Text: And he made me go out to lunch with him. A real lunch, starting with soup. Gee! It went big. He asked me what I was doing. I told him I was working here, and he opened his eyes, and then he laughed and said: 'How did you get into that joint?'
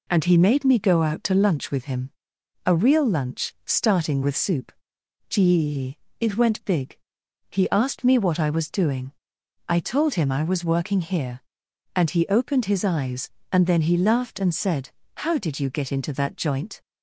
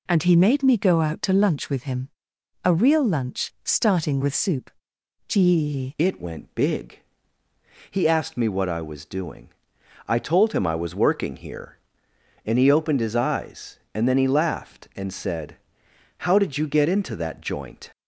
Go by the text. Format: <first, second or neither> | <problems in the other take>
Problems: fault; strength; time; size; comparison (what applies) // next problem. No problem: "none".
first | changes voice at "It"; from 5.9 s on; 12.0 s long